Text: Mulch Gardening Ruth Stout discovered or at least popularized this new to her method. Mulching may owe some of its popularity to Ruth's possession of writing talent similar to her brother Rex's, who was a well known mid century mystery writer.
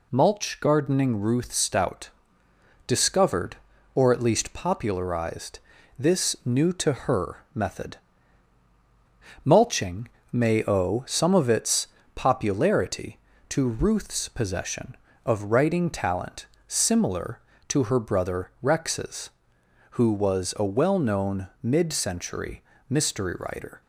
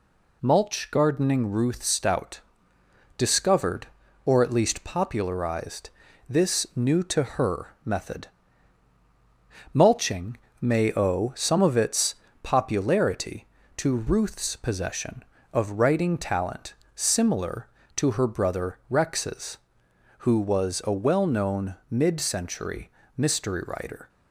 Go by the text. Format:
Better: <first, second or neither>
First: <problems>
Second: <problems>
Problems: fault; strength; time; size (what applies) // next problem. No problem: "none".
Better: neither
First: pauses between "Stout" and "discovered"; noticeable; at 2.0 s; 0.78 s long // pauses between "popularized" and "this"; at 5.5 s; 0.40 s long // pauses between "Mulching" and "may"; slight; at 10.0 s; 0.24 s long // pauses between "its" and "popularity"; slight; at 11.8 s; 0.30 s long // pauses between "talent" and "similar"; slight; at 16.4 s; 0.20 s long // pauses between "known" and "mid"; slight; at 21.4 s; 0.16 s long // pauses between "century" and "mystery"; slight; at 22.6 s; 0.26 s long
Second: pauses between "Stout" and "discovered"; noticeable; at 2.3 s; 0.78 s long // pauses between "popularized" and "this"; at 5.8 s; 0.40 s long // pauses between "Mulching" and "may"; slight; at 10.3 s; 0.24 s long // pauses between "its" and "popularity"; slight; at 12.1 s; 0.30 s long // pauses between "talent" and "similar"; slight; at 16.7 s; 0.20 s long // pauses between "known" and "mid"; slight; at 21.7 s; 0.16 s long // pauses between "century" and "mystery"; slight; at 22.9 s; 0.26 s long